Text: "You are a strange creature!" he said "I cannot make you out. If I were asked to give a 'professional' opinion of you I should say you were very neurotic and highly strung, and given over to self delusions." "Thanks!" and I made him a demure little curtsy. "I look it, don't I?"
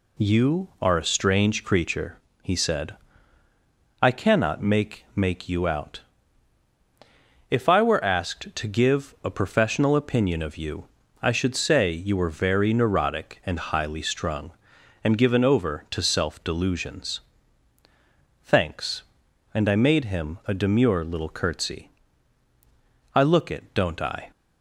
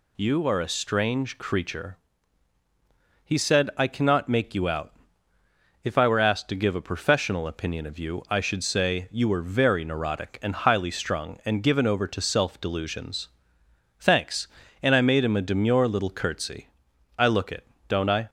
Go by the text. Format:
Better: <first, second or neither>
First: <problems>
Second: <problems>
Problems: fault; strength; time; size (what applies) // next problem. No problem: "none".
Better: second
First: pauses between "said" and "I"; at 2.9 s; 1.0 s long // says "make" twice; at 5.1 s // pauses between "you" and "I"; slight; at 10.8 s; 0.34 s long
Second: none